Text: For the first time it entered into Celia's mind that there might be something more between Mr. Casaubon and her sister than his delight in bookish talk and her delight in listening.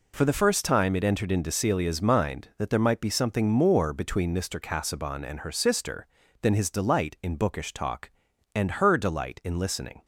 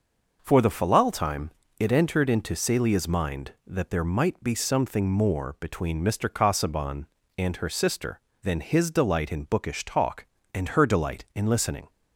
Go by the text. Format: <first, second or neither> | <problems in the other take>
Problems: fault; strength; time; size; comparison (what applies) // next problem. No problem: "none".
first | says "falal" for "first"; at 0.7 s // pauses between "time" and "it"; slight; at 1.5 s; 0.28 s long